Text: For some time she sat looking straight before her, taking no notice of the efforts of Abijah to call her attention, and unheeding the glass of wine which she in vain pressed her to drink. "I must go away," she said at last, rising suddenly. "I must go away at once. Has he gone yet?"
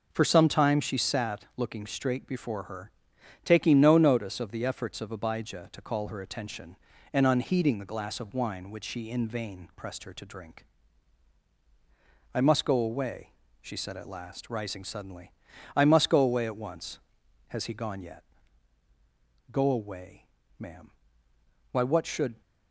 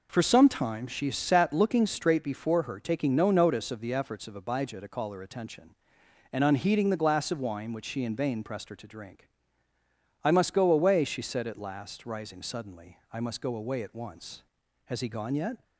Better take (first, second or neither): second